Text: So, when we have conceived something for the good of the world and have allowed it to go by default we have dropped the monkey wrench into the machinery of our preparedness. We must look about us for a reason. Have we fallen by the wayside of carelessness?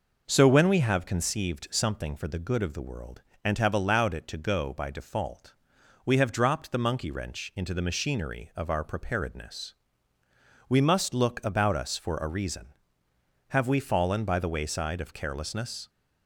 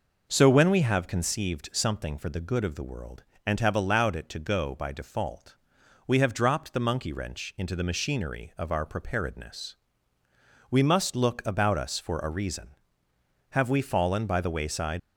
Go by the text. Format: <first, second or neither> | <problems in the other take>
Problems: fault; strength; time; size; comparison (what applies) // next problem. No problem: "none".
first | pauses between "default" and "we"; noticeable; at 5.5 s; 0.50 s long; noticeable in the first // stops before "of carelessness"; at 14.9 s